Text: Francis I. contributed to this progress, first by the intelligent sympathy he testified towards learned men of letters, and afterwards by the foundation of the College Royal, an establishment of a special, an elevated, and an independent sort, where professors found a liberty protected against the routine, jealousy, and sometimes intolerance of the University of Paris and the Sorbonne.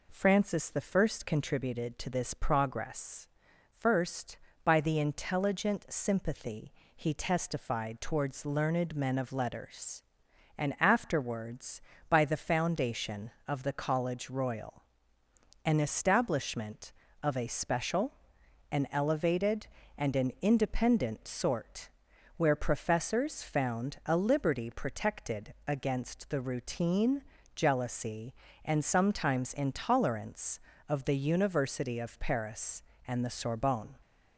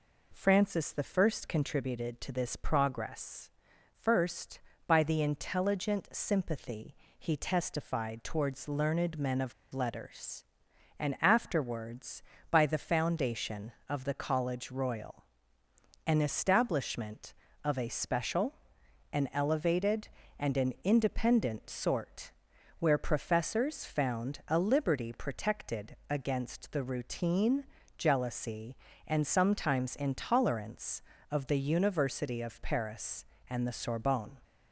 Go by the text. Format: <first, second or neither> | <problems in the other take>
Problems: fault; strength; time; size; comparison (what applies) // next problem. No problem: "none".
first | pauses between "I" and "contributed"; slight; at 1.3 s; 0.16 s long; slight in the first // pauses between "sympathy" and "he"; slight; at 6.9 s; 0.24 s long; slight in the first // pauses between "of" and "letters"; slight; at 9.5 s; 0.19 s long